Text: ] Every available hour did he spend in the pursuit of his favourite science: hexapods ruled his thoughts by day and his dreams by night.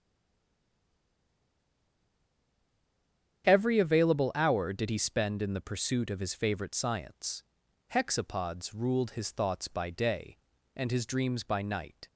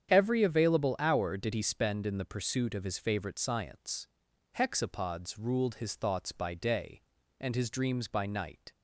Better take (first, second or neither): second